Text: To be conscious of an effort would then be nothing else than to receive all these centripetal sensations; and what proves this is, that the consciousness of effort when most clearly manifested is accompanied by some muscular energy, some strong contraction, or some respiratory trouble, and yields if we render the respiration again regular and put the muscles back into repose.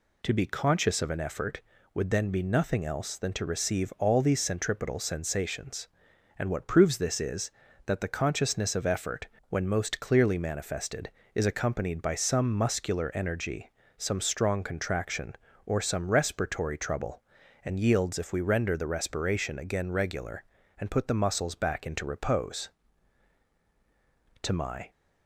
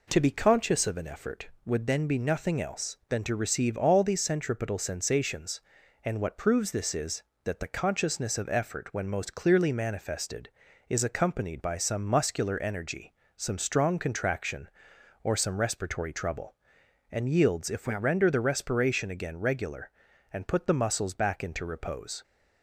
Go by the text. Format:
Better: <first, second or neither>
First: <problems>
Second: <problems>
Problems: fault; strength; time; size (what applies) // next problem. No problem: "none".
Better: second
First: pauses between "effort" and "when"; slight; at 9.2 s; 0.22 s long // goes on to say "To my"; slight; from 24.4 s on; 0.48 s long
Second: none